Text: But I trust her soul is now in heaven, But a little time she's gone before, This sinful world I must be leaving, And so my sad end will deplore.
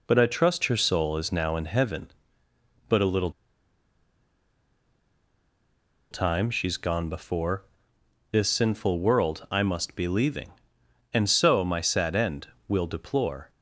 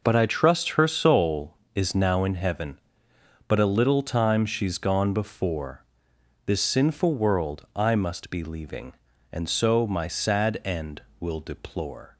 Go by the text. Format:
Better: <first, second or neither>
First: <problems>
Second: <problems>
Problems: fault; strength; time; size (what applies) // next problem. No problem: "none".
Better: second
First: pauses between "little" and "time"; strong; at 3.3 s; 2.7 s long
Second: none